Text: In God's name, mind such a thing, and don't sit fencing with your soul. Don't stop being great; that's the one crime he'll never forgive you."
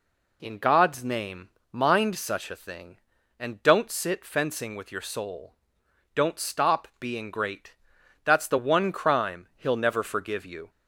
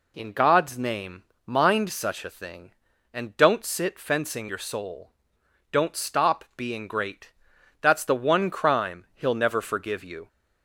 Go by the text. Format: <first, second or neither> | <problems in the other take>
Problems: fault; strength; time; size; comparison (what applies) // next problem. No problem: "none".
first | skips "with"; at 4.4 s